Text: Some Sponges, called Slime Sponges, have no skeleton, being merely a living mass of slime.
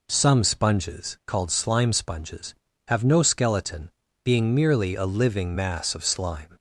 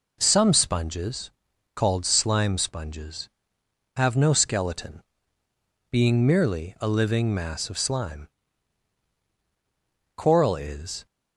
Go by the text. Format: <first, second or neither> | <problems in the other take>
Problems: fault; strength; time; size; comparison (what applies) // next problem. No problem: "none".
first | goes on to say "Coral is"; noticeable; from 10.1 s on; 0.90 s long